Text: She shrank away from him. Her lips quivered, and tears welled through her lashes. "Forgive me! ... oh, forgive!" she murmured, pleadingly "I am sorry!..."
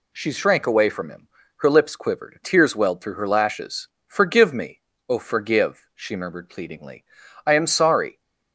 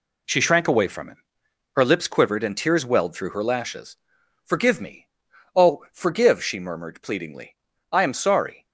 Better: second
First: skips "and"; at 2.4 s // pauses between "pleadingly" and "I"; at 7.0 s; 0.44 s long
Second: pauses between "pleadingly" and "I"; slight; at 7.5 s; 0.34 s long

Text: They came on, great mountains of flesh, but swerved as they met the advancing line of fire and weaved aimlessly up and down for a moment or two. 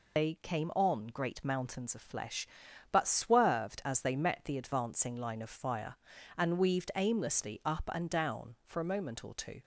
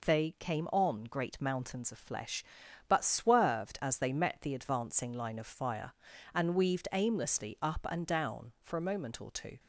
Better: second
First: loses the start of "They"; at 0.1 s; 105 ms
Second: none

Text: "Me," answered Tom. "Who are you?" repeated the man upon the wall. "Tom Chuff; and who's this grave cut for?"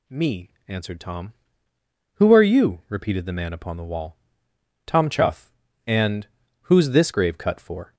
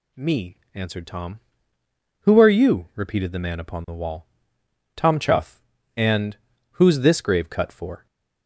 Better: neither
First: pauses between "and" and "who's"; slight; at 6.2 s; 0.34 s long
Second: pauses between "and" and "who's"; slight; at 6.3 s; 0.34 s long

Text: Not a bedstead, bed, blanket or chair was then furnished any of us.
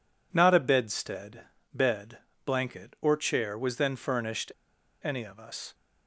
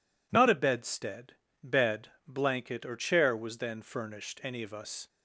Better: second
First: pauses between "furnished" and "any"; noticeable; at 4.5 s; 0.51 s long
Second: none

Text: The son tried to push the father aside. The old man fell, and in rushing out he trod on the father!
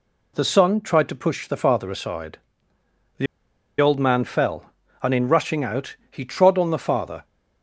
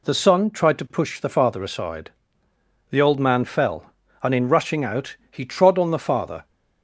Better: second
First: pauses between "The" and "old"; noticeable; at 3.2 s; 0.54 s long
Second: none

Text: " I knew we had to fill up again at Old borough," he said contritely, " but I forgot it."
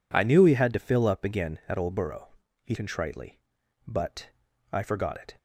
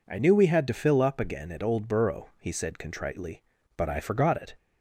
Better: second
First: skips "said"; at 2.7 s // pauses between "but" and "I"; at 4.3 s; 0.40 s long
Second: none

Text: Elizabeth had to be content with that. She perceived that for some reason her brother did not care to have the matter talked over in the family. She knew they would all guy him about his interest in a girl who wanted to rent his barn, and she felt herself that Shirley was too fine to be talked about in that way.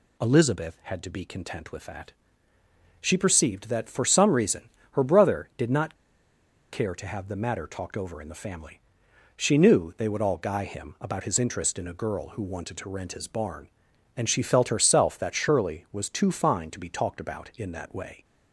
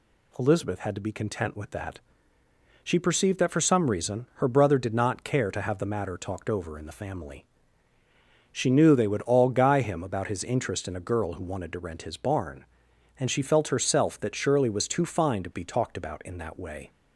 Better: second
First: pauses between "reason" and "her"; slight; at 4.6 s; 0.24 s long // pauses between "not" and "care"; noticeable; at 5.9 s; 0.78 s long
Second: none

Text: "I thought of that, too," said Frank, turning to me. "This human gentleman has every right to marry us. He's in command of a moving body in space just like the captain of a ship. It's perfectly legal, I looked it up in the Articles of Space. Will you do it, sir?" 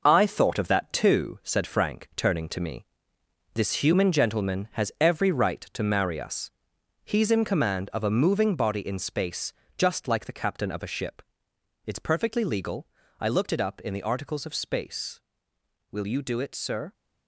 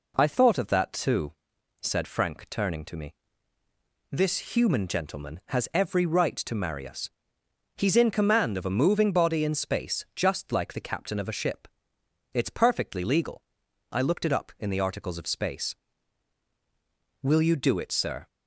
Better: second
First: gets quieter; strong; throughout; 7.5 dB // pauses between "space" and "just"; slight; at 9.5 s; 0.24 s long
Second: none

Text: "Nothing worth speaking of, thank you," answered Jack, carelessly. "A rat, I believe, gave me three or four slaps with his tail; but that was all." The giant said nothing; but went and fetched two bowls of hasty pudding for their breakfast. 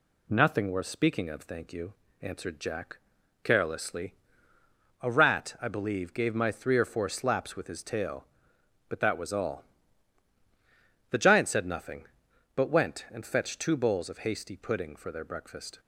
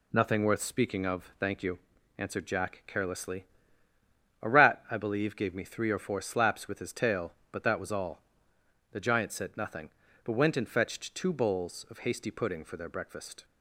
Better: second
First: says "my" for "me"; at 6.3 s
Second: none

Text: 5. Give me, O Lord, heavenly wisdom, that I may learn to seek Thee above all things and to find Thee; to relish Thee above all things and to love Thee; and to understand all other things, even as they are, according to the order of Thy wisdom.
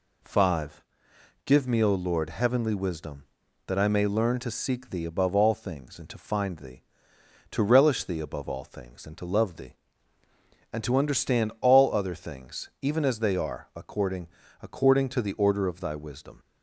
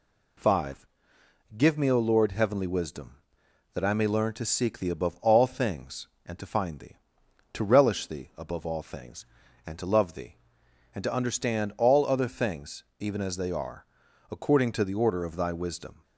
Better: second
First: says "according" twice; at 14.6 s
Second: none

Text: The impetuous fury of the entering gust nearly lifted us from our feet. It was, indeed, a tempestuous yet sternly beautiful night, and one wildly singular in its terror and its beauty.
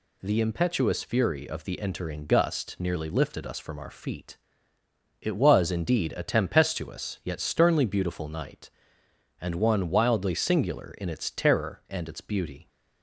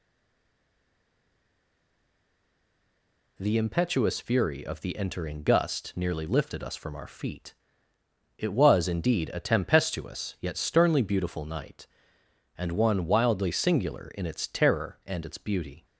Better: first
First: none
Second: stays silent before the first word; strong; until 3.3 s; 3.3 s long

